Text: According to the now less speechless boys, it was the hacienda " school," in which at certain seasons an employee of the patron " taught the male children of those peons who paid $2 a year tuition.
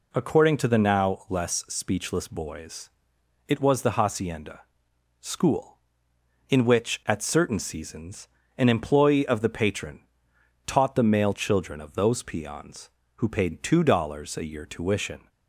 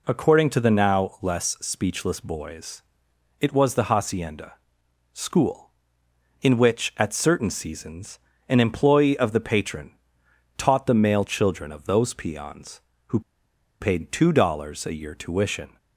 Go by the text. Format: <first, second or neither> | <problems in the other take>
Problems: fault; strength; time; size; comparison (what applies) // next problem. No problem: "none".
first | pauses between "seasons" and "an"; slight; at 8.1 s; 0.30 s long; slight in the first // pauses between "who" and "paid"; noticeable; at 13.1 s; 0.61 s long